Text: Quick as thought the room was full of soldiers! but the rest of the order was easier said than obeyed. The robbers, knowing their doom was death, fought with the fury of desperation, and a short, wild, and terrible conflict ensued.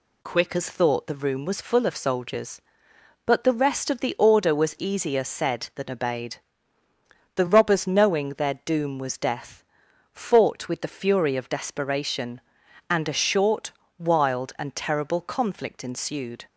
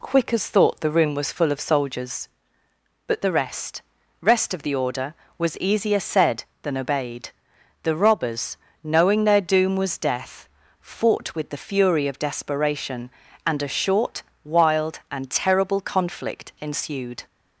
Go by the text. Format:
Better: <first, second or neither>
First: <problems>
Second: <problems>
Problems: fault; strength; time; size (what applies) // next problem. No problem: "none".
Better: first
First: none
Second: says "rest" twice; at 4.1 s